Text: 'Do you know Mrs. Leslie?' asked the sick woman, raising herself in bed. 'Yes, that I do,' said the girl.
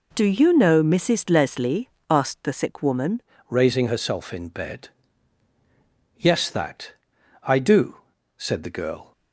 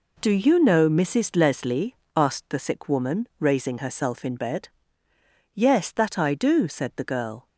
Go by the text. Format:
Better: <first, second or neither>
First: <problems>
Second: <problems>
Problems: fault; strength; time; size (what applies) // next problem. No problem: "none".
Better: second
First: changes voice at "raising"; from 3.4 s on; 5.7 s long // pauses between "that" and "I"; noticeable; at 6.9 s; 0.50 s long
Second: none